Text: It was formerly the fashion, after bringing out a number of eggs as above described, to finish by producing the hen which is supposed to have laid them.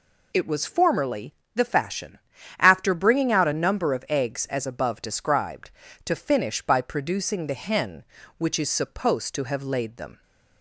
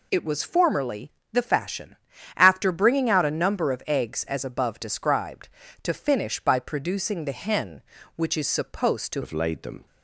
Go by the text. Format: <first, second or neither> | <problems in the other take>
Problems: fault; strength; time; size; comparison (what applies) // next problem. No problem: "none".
first | pauses between "formerly" and "the"; slight; at 1.1 s; 0.20 s long; slight in the first // changes voice at "have"; from 9.2 s on; 0.6 s long